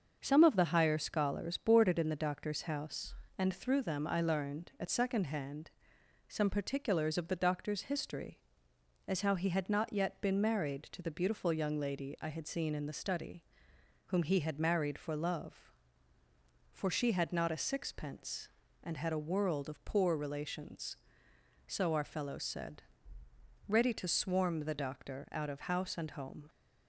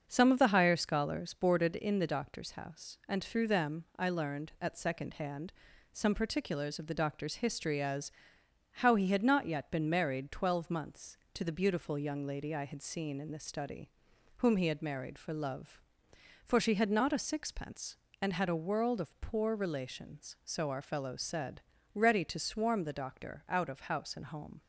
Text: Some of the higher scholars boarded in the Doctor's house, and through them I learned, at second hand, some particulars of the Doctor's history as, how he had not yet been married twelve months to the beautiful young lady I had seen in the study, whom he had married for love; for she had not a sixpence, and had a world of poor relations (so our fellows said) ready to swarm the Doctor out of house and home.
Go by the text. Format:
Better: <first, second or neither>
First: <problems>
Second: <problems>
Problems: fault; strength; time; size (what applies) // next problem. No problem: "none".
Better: second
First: starts louder than the rest; until 1.2 s; 6.5 dB // skips "twelve months"; at 10.8 s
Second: starts louder than the rest; until 1.0 s; 6.5 dB